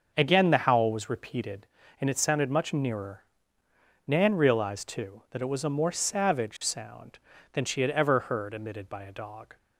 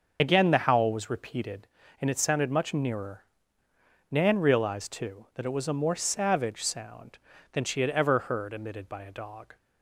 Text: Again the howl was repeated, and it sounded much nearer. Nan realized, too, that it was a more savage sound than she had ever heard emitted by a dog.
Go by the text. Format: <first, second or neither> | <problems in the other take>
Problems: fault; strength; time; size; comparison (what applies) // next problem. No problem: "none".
first | loses the start of "Again"; at 0.1 s; 45 ms // starts louder than the rest; until 1.2 s; 6.5 dB; also in the first